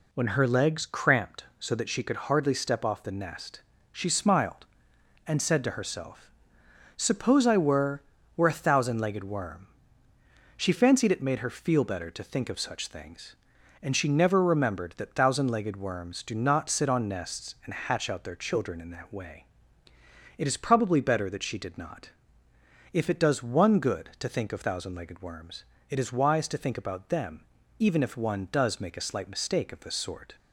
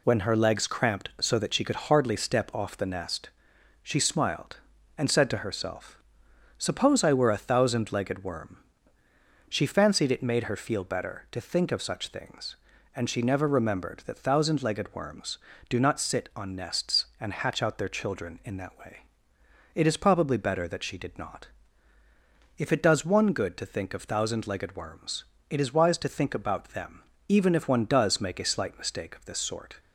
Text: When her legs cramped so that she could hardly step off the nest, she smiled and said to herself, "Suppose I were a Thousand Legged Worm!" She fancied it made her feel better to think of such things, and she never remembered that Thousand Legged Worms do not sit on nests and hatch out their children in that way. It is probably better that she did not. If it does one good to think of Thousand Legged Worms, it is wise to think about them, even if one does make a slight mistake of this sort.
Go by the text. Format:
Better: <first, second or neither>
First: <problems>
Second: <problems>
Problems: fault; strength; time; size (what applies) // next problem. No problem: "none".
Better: second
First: says "were" twice; at 8.3 s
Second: none